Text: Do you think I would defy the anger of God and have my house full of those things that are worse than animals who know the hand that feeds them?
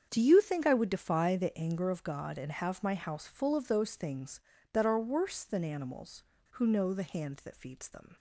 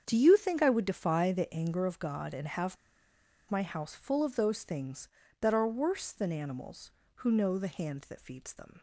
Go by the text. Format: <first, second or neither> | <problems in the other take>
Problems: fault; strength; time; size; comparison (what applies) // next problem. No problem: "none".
first | starts louder than the rest; strong; until 1.0 s; 7.5 dB; strong in the first // pauses between "have" and "my"; noticeable; at 2.7 s; 0.74 s long